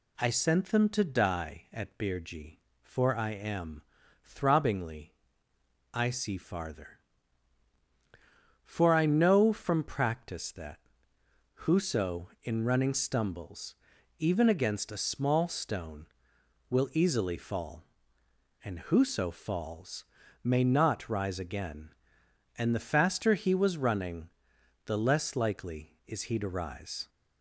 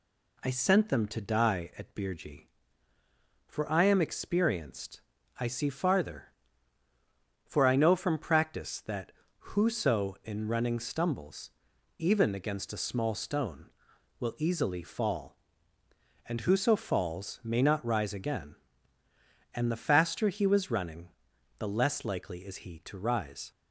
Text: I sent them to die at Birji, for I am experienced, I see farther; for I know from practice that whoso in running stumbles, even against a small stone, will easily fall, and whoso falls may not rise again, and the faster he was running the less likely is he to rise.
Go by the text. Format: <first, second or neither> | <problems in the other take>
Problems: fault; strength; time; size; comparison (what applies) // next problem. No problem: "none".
second | says "throbbingly" for "experienced"; at 4.2 s // pauses between "that" and "whoso"; noticeable; at 10.7 s; 0.86 s long; slight in the second // pauses between "falls" and "may"; at 20.0 s; 0.40 s long // pauses between "running" and "the"; noticeable; at 24.2 s; 0.56 s long; noticeable in the second